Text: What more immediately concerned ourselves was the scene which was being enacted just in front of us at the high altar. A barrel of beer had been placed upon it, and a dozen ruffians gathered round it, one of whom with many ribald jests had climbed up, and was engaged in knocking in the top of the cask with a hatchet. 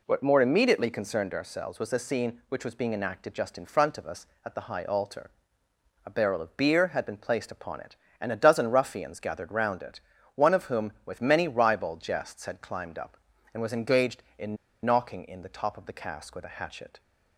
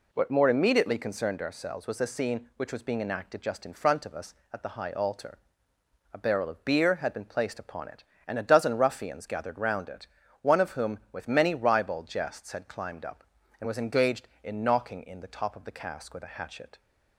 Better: second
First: pauses between "in" and "knocking"; slight; at 14.5 s; 0.27 s long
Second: none

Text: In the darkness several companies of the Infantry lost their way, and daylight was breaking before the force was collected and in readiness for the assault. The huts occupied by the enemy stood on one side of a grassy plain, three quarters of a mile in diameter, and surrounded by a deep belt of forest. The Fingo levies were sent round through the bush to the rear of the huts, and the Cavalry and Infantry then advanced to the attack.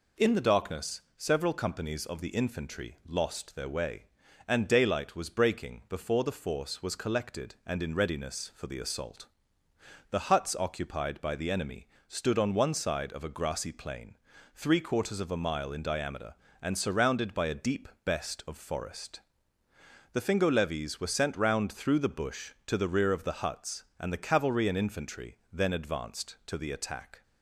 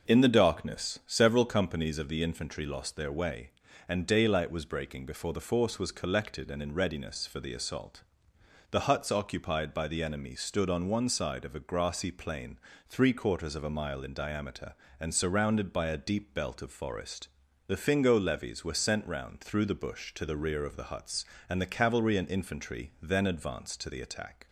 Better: second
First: pauses between "darkness" and "several"; slight; at 1.0 s; 0.16 s long // pauses between "enemy" and "stood"; slight; at 11.8 s; 0.22 s long // says "best" for "belt"; at 18.0 s // pauses between "Infantry" and "then"; slight; at 25.3 s; 0.16 s long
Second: none

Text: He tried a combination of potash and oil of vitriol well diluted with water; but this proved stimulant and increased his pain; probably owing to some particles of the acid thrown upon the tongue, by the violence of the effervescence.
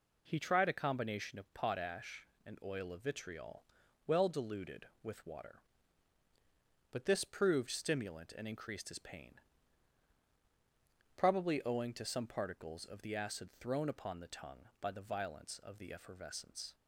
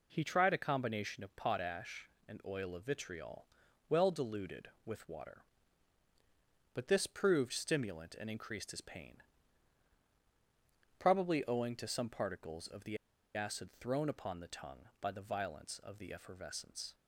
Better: first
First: pauses between "vitriol" and "well"; at 3.6 s; 0.42 s long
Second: pauses between "vitriol" and "well"; at 3.4 s; 0.42 s long // pauses between "the" and "acid"; at 12.9 s; 0.37 s long

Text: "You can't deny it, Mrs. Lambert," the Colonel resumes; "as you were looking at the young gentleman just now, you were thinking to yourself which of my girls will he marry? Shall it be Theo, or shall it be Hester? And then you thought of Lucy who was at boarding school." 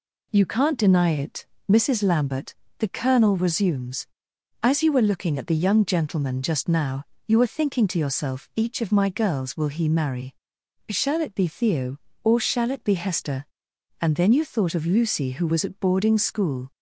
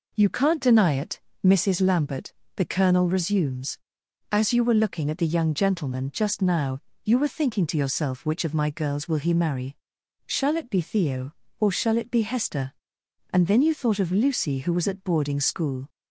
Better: second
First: says "each" for "which"; at 8.5 s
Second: none

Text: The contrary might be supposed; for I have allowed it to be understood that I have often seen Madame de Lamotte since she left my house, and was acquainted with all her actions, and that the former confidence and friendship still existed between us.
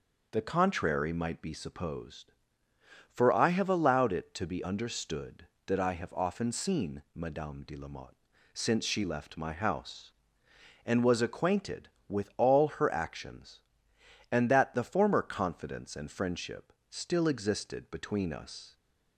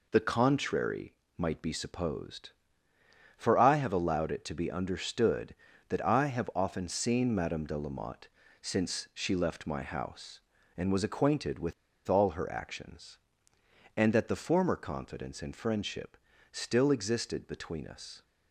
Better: first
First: pauses between "Lamotte" and "since"; slight; at 8.1 s; 0.36 s long // pauses between "friendship" and "still"; slight; at 16.7 s; 0.16 s long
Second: pauses between "contrary" and "might"; slight; at 1.1 s; 0.24 s long // pauses between "Lamotte" and "since"; slight; at 8.2 s; 0.34 s long // pauses between "with" and "all"; slight; at 11.7 s; 0.34 s long // pauses between "friendship" and "still"; slight; at 16.1 s; 0.36 s long

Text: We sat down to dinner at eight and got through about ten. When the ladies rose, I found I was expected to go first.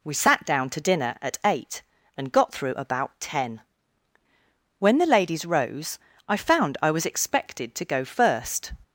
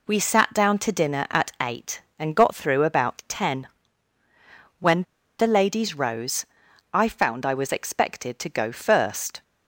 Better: first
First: none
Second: pauses between "When" and "the"; slight; at 5.0 s; 0.35 s long

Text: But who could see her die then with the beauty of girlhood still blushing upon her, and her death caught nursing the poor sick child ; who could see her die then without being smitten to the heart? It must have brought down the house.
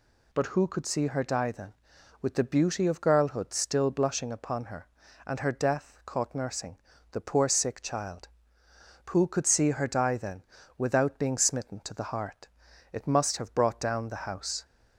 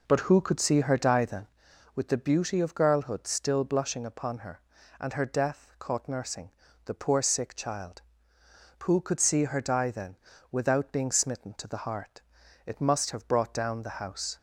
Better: first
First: pauses between "nursing" and "the"; slight; at 6.7 s; 0.34 s long // pauses between "then" and "without"; slight; at 10.4 s; 0.34 s long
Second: starts louder than the rest; noticeable; until 1.6 s; 4.5 dB // pauses between "nursing" and "the"; slight; at 6.5 s; 0.34 s long // pauses between "then" and "without"; slight; at 10.1 s; 0.34 s long

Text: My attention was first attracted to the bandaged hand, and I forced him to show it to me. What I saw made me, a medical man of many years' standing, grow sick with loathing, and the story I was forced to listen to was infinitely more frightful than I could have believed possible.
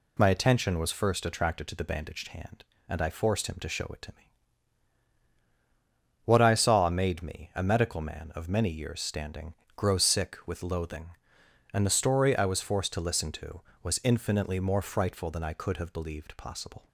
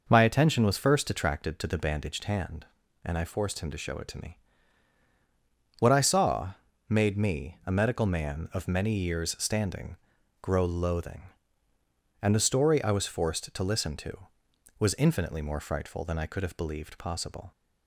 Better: first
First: none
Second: pauses between "saw" and "made"; slight; at 6.5 s; 0.36 s long // skips "sick with"; at 10.6 s

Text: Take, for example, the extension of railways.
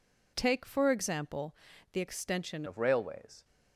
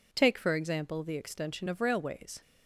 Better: second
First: changes voice at "of"; from 2.6 s on; 0.8 s long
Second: none

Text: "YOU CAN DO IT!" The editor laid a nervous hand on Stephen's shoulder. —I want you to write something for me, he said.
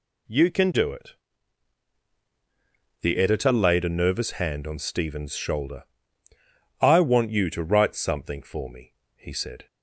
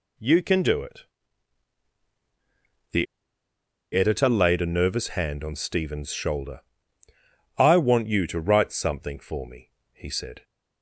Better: first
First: none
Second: pauses between "The" and "editor"; noticeable; at 3.0 s; 0.87 s long

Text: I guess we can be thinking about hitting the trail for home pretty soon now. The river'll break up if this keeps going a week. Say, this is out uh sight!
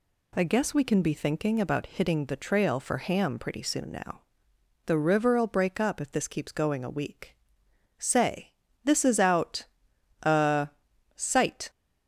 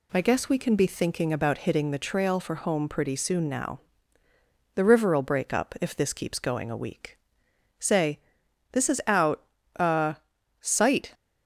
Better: second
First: says "ham" for "home"; at 2.9 s // pauses between "out" and "uh"; noticeable; at 9.6 s; 0.58 s long // pauses between "uh" and "sight"; noticeable; at 10.6 s; 0.50 s long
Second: pauses between "out" and "uh"; slight; at 9.4 s; 0.36 s long // pauses between "uh" and "sight"; noticeable; at 10.1 s; 0.46 s long

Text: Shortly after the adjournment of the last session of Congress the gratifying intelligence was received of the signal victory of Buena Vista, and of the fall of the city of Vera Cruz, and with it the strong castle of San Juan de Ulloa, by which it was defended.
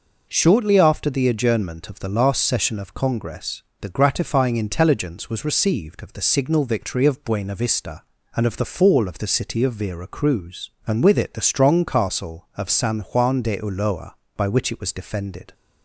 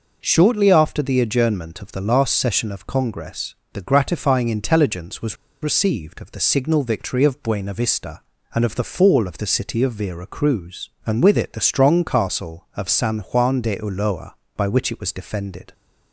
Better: first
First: pauses between "Congress" and "the"; slight; at 3.6 s; 0.18 s long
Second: pauses between "Congress" and "the"; slight; at 3.5 s; 0.18 s long // pauses between "was" and "received"; slight; at 5.3 s; 0.26 s long

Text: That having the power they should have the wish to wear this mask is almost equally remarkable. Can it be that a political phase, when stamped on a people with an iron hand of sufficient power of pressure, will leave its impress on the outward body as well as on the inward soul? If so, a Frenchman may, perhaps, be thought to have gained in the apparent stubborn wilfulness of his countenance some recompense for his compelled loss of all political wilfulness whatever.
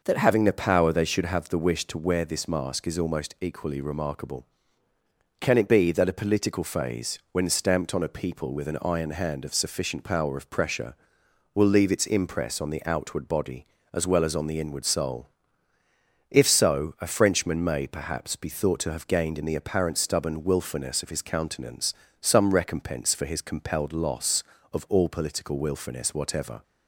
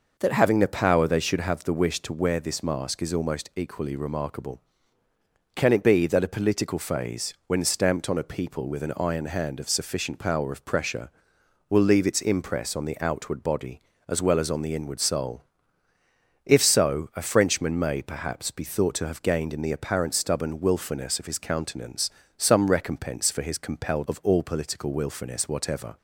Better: first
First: pauses between "countenance" and "some"; slight; at 21.9 s; 0.28 s long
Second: pauses between "countenance" and "some"; slight; at 22.0 s; 0.28 s long // skips "loss"; at 24.0 s

